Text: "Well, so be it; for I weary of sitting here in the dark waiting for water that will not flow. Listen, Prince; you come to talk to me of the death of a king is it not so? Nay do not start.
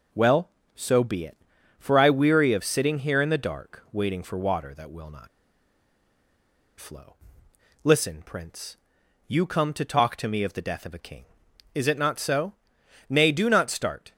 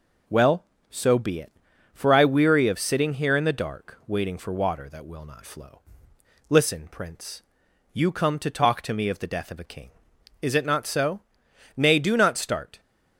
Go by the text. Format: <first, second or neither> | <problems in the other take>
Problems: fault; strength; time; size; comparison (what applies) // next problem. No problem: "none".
second | pauses between "not" and "flow"; strong; at 5.2 s; 1.5 s long